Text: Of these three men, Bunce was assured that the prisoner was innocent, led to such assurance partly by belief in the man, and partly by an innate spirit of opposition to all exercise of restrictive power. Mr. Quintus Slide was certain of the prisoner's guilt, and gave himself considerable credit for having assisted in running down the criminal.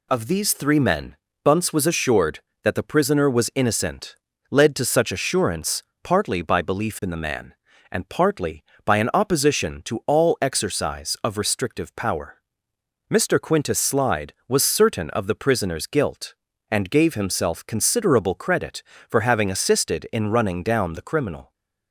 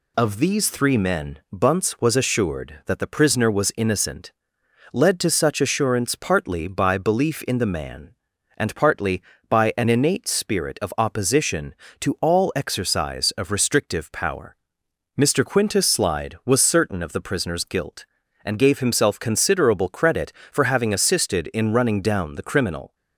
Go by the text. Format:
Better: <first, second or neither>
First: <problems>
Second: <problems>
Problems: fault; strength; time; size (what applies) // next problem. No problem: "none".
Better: second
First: pauses between "assurance" and "partly"; slight; at 5.8 s; 0.20 s long // skips "innate spirit of"; at 9.1 s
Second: none